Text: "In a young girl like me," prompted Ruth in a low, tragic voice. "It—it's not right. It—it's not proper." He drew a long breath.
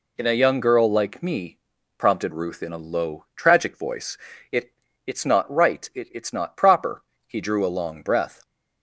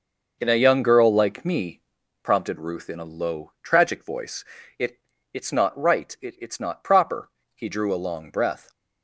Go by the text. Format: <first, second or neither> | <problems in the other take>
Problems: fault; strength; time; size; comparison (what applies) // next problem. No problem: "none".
first | starts louder than the rest; noticeable; until 2.0 s; 5.5 dB